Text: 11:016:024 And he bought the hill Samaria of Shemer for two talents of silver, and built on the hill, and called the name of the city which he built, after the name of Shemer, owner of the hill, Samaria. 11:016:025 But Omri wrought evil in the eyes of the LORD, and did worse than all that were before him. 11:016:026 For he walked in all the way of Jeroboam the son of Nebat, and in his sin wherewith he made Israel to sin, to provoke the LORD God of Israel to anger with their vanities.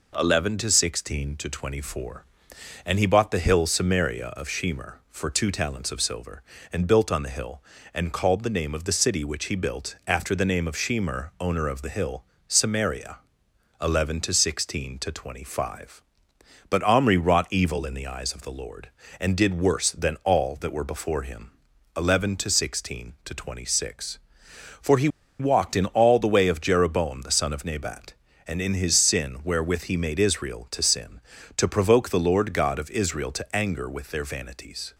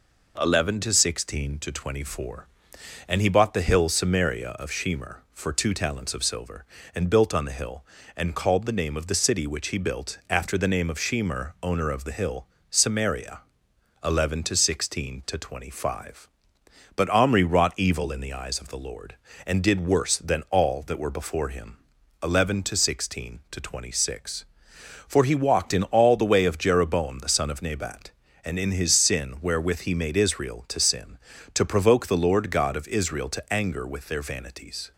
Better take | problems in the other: second | pauses between "he" and "walked"; slight; at 25.0 s; 0.31 s long

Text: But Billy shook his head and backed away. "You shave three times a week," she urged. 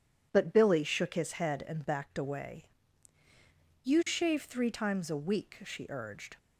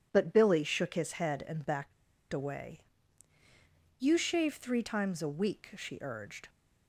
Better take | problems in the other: first | pauses between "backed" and "away"; at 1.9 s; 0.37 s long

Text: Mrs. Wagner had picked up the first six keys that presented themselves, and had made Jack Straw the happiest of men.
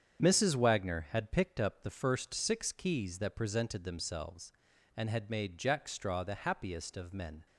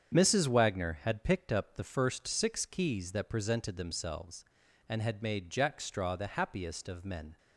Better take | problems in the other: neither | starts louder than the rest; strong; the same in both

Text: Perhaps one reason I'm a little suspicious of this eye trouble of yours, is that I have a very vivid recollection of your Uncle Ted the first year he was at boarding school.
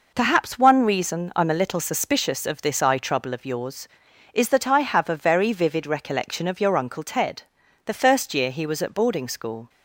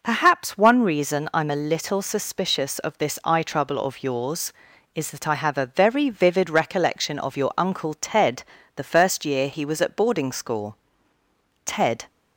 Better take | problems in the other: first | pauses between "Ted" and "the"; slight; at 8.4 s; 0.34 s long; also in the first // goes on to say "Ted"; slight; from 11.6 s on; 0.42 s long

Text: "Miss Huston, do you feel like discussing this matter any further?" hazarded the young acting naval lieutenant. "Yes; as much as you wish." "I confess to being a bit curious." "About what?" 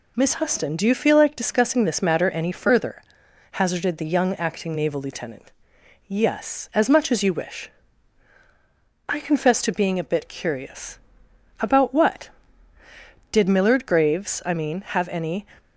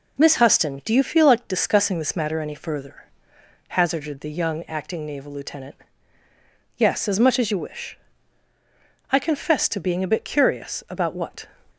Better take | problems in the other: second | goes on to say "Did Millard Graves I mean have any"; strong; from 13.3 s on; 2.1 s long

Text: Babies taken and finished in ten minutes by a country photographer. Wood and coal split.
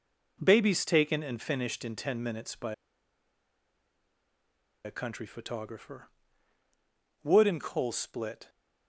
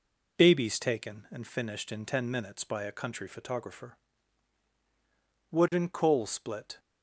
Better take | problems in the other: second | pauses between "by" and "a"; strong; at 2.7 s; 2.1 s long

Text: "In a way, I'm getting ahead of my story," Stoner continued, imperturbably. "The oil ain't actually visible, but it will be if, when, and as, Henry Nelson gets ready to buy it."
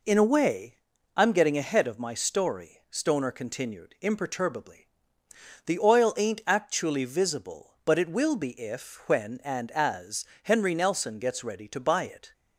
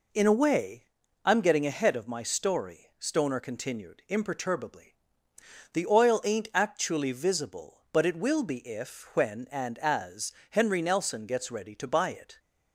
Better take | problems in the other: neither | none

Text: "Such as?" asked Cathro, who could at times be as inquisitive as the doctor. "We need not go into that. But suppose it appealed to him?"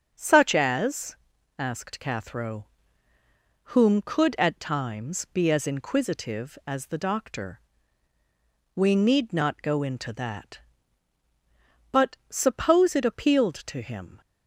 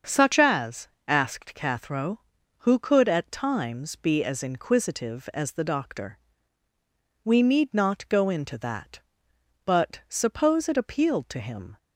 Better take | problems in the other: second | starts louder than the rest; strong; until 1.1 s; 7.5 dB; also in the second // says "whom" for "who"; at 3.6 s

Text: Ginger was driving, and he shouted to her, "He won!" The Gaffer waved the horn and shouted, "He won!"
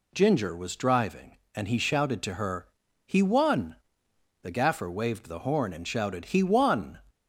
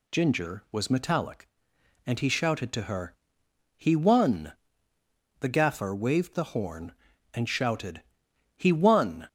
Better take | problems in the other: first | says "metallic" for "driving"; at 0.8 s

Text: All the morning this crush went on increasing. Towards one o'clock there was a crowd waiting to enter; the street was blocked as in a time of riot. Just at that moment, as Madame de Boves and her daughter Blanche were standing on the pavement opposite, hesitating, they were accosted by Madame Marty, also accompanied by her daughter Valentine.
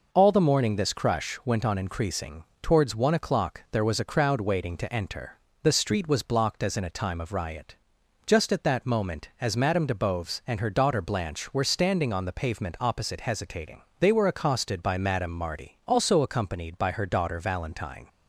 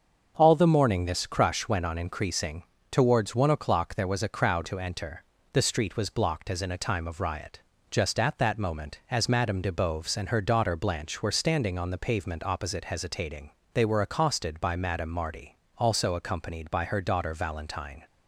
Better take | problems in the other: first | starts louder than the rest; until 1.3 s; 6.5 dB // skips "waiting"; at 4.6 s

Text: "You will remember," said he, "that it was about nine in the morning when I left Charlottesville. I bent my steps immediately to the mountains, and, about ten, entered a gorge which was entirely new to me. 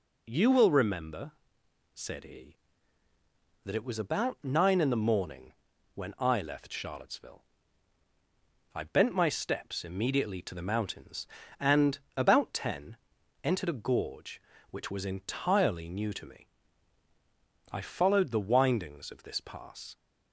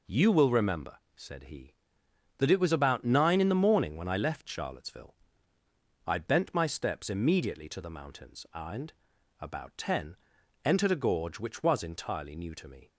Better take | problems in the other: second | pauses between "morning" and "when"; at 5.5 s; 0.44 s long // goes on to say "I followed the windings of this pass"; strong; from 17.7 s on; 2.2 s long

